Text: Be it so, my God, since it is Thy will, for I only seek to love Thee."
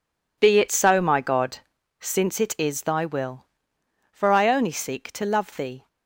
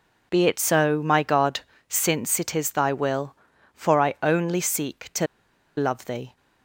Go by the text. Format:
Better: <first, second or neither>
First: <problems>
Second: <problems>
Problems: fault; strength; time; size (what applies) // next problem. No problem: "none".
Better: first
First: none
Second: pauses between "to" and "love"; noticeable; at 5.2 s; 0.51 s long